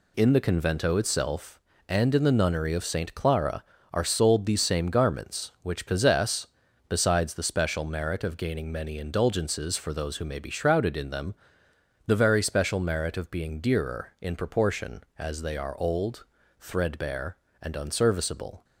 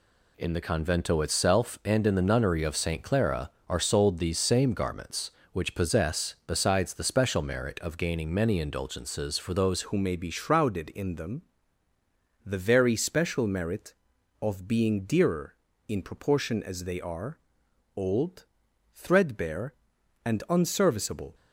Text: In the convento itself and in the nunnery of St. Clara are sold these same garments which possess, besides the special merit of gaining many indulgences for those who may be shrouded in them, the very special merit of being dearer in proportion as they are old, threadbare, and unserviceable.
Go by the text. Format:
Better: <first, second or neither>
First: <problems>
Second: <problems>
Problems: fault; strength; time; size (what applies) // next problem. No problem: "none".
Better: first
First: none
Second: changes voice at "who"; from 9.8 s on; 11.5 s long // pauses between "are" and "old"; noticeable; at 17.3 s; 0.58 s long